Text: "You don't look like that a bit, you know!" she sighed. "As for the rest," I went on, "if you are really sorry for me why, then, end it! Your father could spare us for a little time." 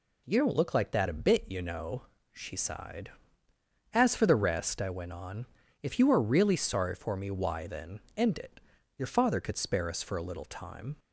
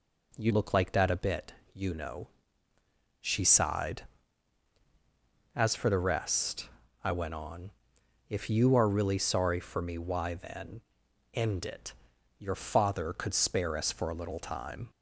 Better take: first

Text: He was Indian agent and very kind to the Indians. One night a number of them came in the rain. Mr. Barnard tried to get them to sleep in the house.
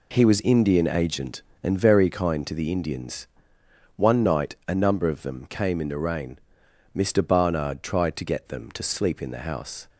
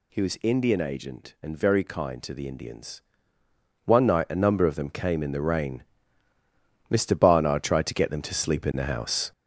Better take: first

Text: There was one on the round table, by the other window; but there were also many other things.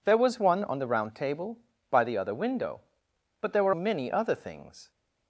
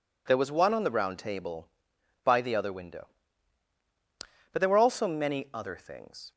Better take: second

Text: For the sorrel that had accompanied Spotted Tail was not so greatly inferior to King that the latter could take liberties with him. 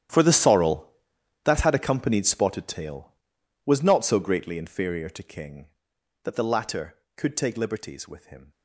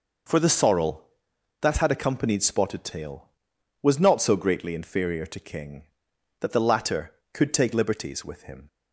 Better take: second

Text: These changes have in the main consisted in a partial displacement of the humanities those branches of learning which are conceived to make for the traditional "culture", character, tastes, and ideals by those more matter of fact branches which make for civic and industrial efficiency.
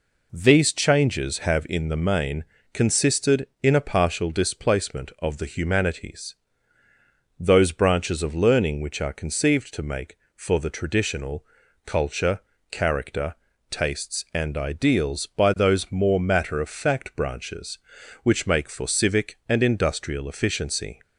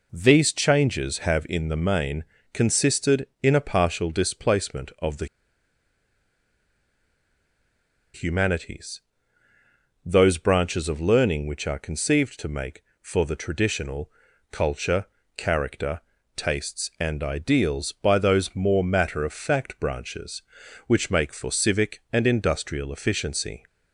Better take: first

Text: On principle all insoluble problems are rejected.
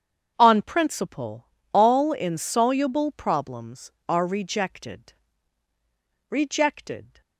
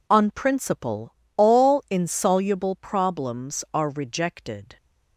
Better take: second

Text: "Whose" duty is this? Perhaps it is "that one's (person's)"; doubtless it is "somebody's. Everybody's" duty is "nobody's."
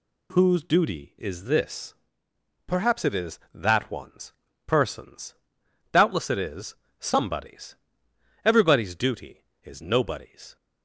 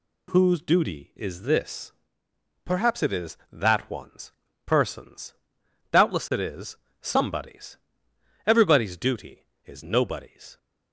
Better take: neither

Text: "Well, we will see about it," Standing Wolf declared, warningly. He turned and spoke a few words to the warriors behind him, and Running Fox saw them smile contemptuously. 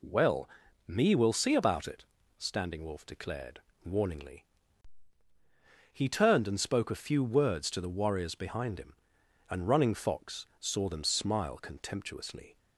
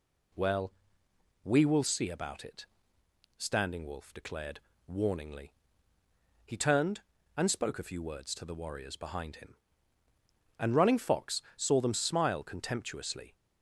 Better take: second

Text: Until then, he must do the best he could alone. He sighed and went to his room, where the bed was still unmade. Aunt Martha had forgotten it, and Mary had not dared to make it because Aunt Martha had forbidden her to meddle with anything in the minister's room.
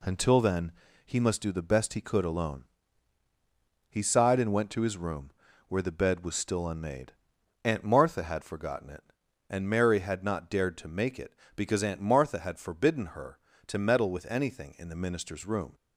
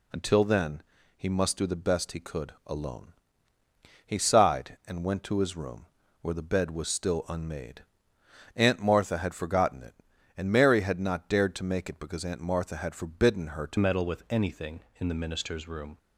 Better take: first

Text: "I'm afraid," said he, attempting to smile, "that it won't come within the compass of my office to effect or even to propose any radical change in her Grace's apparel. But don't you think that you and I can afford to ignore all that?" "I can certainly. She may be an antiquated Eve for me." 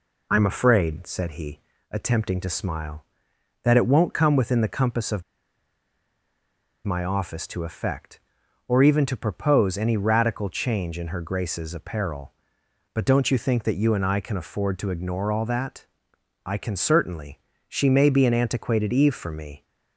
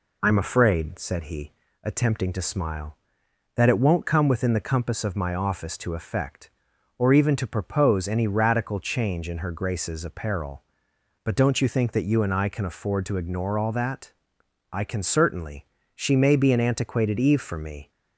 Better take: second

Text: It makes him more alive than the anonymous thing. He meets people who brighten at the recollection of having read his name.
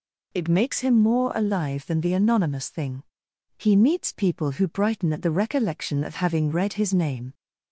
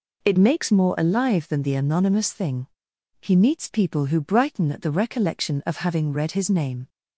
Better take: first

